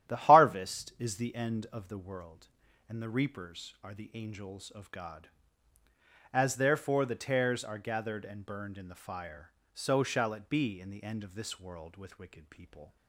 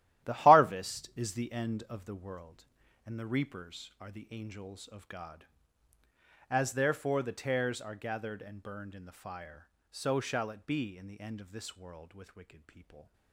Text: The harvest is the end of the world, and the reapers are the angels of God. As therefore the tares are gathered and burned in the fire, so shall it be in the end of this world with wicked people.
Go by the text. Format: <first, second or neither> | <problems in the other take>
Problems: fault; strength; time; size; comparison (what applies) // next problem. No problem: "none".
first | gets quieter; strong; throughout; 12 dB // starts louder than the rest; strong; until 1.3 s; 13.5 dB; strong in the first